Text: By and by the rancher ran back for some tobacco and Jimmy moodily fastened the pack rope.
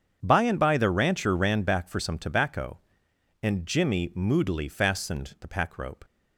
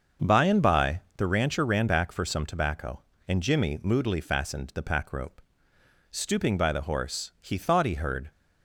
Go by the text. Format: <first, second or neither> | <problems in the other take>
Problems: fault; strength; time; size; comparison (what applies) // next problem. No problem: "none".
first | starts louder than the rest; until 1.3 s; 6.5 dB; strong in the first // pauses between "by" and "the"; slight; at 1.0 s; 0.16 s long // goes on to say "Stooping by the horse he thought he heard"; strong; from 6.1 s on; 2.1 s long